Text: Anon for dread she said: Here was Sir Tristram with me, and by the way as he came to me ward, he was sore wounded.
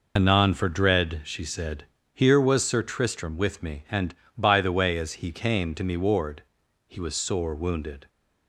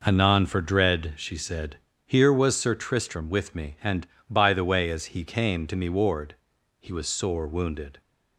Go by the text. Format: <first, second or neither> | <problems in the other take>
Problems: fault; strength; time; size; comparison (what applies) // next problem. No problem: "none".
second | loses the start of "Anon"; at 0.1 s; 65 ms